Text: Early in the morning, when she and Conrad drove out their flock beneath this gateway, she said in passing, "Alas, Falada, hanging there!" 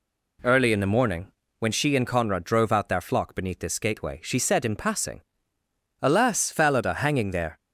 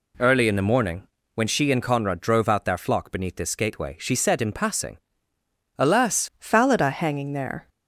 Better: first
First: none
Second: changes voice at "Falada"; from 6.3 s on; 1.3 s long

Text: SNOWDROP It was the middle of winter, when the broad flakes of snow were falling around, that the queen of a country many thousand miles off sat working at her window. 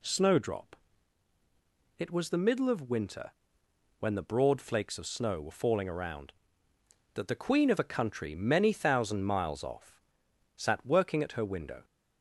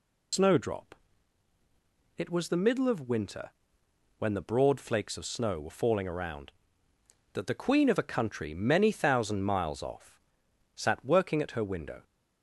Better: first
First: pauses between "SNOWDROP" and "It"; at 0.7 s; 1.2 s long // pauses between "off" and "sat"; noticeable; at 10.0 s; 0.54 s long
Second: loses the start of "SNOWDROP"; at 0.3 s; 115 ms // pauses between "SNOWDROP" and "It"; at 0.9 s; 1.2 s long // pauses between "off" and "sat"; noticeable; at 10.2 s; 0.54 s long

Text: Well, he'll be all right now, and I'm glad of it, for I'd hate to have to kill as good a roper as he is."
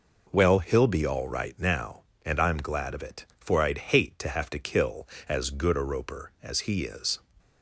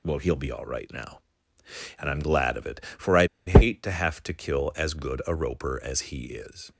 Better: first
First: none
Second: pauses between "I'd" and "hate"; slight; at 3.2 s; 0.21 s long

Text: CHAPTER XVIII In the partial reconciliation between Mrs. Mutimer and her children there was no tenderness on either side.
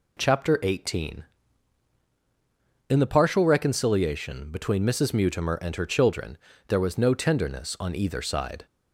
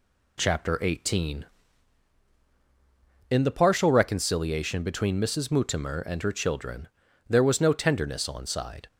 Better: first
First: pauses between "children" and "there"; slight; at 6.3 s; 0.32 s long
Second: pauses between "children" and "there"; at 6.8 s; 0.42 s long // skips "either"; at 8.4 s

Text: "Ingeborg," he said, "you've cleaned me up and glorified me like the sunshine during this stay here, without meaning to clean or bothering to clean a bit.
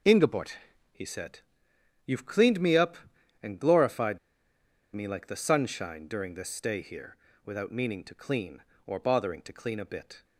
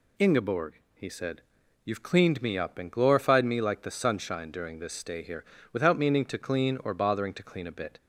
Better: second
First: pauses between "glorified" and "me"; noticeable; at 4.1 s; 0.76 s long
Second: none

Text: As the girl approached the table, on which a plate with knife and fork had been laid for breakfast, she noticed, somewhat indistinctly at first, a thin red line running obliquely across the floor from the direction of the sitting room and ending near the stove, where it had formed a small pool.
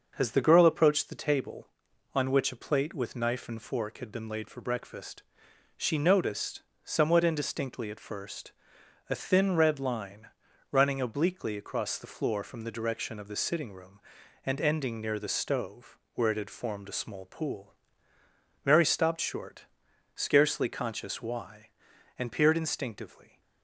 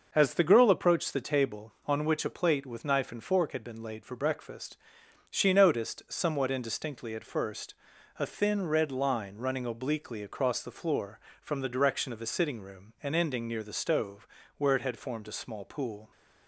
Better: second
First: starts louder than the rest; until 1.1 s; 6 dB // pauses between "line" and "running"; at 10.2 s; 0.42 s long // goes on to say "Mary stopped short scarcely conscious why and peered instinctively"; strong; from 18.6 s on; 4.7 s long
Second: none

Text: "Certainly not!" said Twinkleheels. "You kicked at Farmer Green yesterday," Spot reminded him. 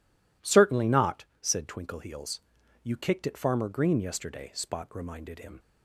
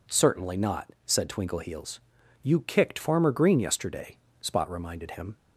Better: first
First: none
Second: skips "at"; at 2.9 s

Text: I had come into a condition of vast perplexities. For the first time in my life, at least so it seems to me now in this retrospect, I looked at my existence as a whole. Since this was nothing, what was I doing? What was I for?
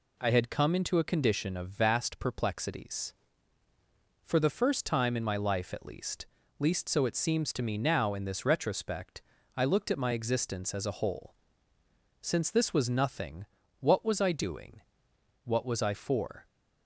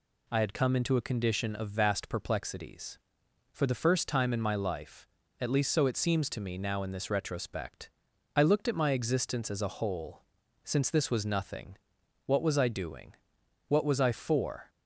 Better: second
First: says "least" twice; at 6.5 s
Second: none

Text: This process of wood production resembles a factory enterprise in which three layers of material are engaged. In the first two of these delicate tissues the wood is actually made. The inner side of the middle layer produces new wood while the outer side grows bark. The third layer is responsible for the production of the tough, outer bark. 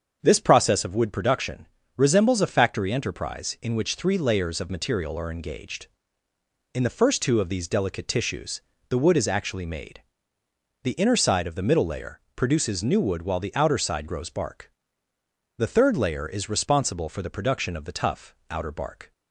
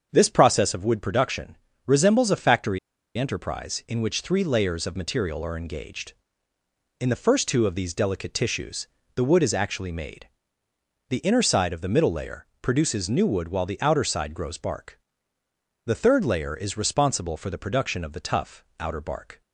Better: first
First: starts louder than the rest; until 1.2 s; 7 dB // pauses between "production" and "resembles"; slight; at 1.6 s; 0.30 s long // pauses between "tissues" and "the"; slight; at 8.5 s; 0.30 s long // pauses between "layer" and "produces"; slight; at 12.1 s; 0.16 s long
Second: starts louder than the rest; until 1.1 s; 7 dB // pauses between "production" and "resembles"; slight; at 1.5 s; 0.30 s long // pauses between "factory" and "enterprise"; at 2.7 s; 0.39 s long // pauses between "tissues" and "the"; slight; at 8.8 s; 0.30 s long // pauses between "layer" and "produces"; slight; at 12.4 s; 0.16 s long

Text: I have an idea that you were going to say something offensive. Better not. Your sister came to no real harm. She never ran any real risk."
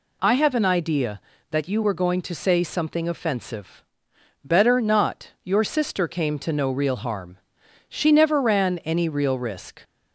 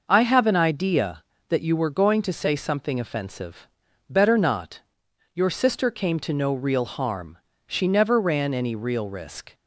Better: neither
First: none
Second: none

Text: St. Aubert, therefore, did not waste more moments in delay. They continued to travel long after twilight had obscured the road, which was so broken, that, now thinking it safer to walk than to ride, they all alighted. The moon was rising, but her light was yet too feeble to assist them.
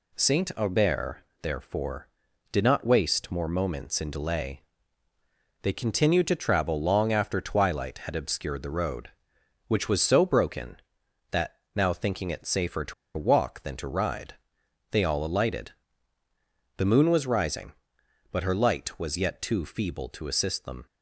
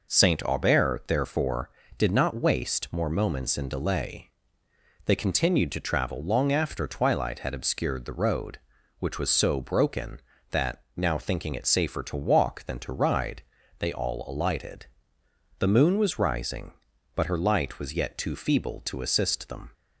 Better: second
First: pauses between "to" and "walk"; slight; at 12.9 s; 0.23 s long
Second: none

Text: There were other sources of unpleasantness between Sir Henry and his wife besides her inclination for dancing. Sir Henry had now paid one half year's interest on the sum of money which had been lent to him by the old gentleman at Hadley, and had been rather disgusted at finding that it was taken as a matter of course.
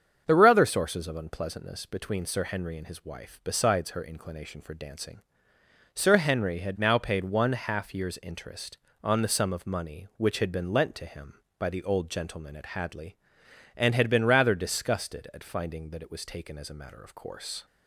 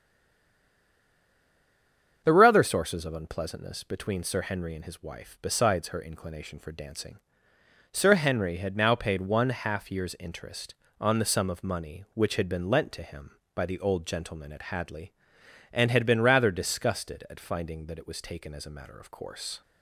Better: first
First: starts louder than the rest; strong; until 1.2 s; 7 dB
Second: stays silent before the first word; until 2.2 s; 2.2 s long // starts louder than the rest; strong; until 3.2 s; 7 dB

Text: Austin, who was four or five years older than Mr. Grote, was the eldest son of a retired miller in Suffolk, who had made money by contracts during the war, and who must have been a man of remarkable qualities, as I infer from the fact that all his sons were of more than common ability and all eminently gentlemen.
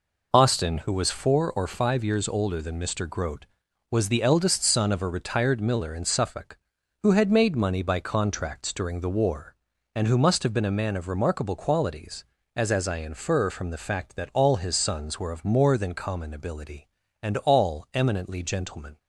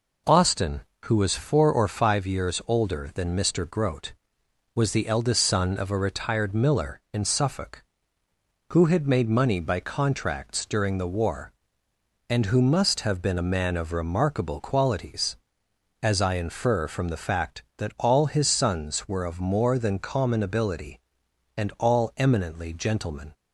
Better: second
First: says "as" twice; at 12.7 s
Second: none

